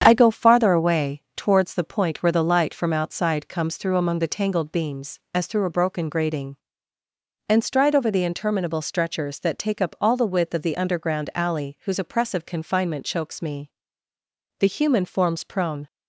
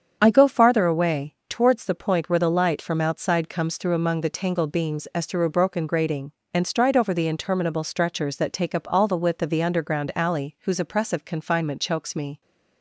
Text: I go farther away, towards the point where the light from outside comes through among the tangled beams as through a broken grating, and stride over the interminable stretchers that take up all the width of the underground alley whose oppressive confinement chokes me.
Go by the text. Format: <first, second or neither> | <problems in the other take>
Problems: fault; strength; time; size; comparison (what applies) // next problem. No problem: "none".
second | starts louder than the rest; strong; until 1.0 s; 8 dB; strong in the second // goes on to say "The human forms prone"; noticeable; from 14.5 s on; 1.2 s long